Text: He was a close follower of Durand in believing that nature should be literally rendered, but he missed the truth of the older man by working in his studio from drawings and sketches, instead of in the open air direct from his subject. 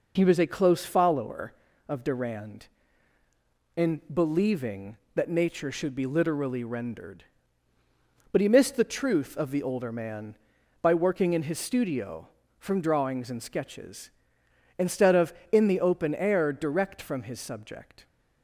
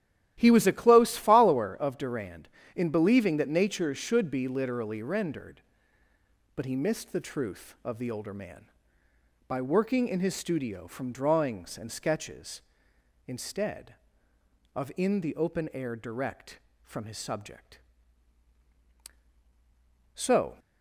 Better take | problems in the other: first | starts louder than the rest; strong; until 1.4 s; 13 dB // goes on to say "So"; slight; from 20.1 s on; 0.44 s long

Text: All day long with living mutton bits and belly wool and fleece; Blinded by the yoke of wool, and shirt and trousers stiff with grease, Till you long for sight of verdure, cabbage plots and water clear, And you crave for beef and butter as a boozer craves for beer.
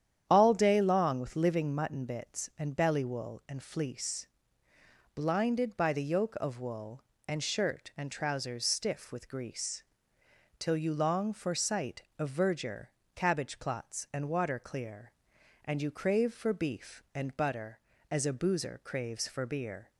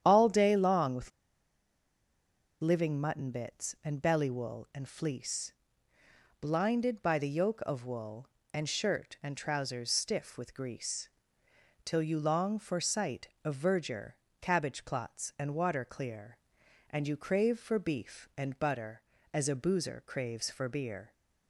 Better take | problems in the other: first | starts louder than the rest; strong; until 1.0 s; 9.5 dB; strong in the first // pauses between "with" and "living"; strong; at 1.1 s; 1.5 s long

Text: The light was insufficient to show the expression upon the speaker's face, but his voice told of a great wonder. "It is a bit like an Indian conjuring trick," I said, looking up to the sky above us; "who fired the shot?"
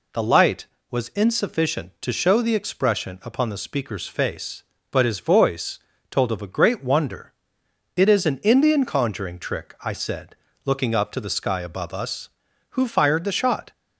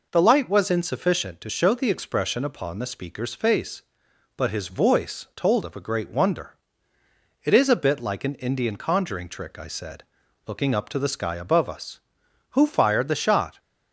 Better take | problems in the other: second | pauses between "voice" and "told"; slight; at 5.7 s; 0.30 s long // skips "a bit like"; at 8.2 s

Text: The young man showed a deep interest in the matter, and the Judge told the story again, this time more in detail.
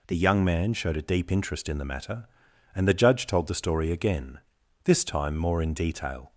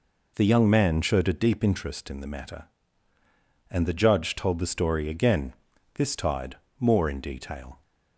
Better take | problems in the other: first | says "tide" for "time"; at 6.1 s

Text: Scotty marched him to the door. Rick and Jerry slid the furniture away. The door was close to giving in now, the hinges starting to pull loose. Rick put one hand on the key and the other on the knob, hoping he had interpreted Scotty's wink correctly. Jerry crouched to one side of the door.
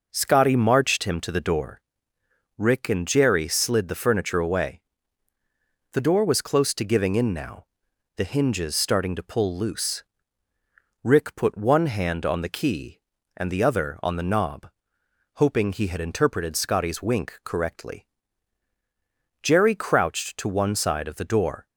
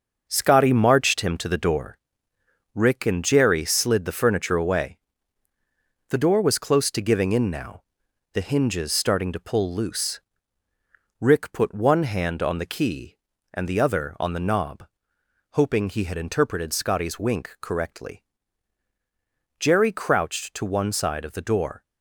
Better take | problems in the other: first | gets quieter; strong; throughout; 7 dB

